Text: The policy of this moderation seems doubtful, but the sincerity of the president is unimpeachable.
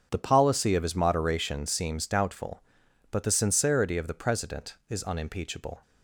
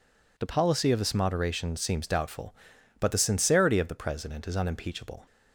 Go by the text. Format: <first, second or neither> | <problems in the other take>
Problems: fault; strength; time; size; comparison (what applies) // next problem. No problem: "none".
second | starts louder than the rest; strong; until 1.1 s; 7.5 dB // says "his" for "this"; at 0.8 s